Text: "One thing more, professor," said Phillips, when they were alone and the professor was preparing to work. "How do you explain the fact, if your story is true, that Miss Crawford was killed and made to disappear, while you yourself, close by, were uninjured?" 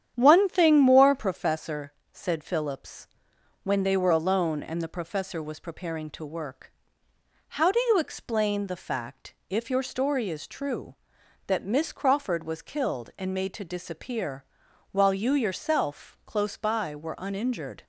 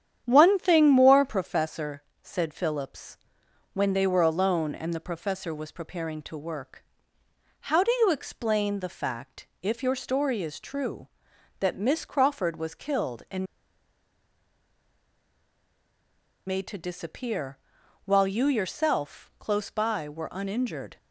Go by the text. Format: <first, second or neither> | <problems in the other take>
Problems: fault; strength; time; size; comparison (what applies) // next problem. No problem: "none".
first | starts louder than the rest; strong; until 1.2 s; 9.5 dB; strong in the first // pauses between "and" and "made"; strong; at 13.4 s; 3.0 s long